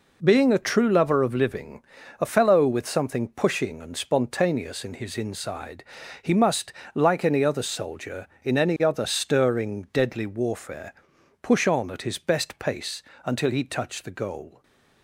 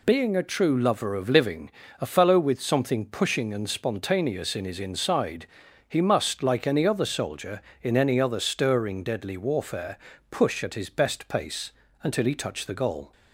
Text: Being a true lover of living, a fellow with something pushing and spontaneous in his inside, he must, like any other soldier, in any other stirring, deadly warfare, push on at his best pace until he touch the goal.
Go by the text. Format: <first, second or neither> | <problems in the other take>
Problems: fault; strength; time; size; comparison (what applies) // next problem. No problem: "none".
first | skips "on"; at 10.6 s // pauses between "pace" and "until"; slight; at 11.6 s; 0.32 s long; slight in the first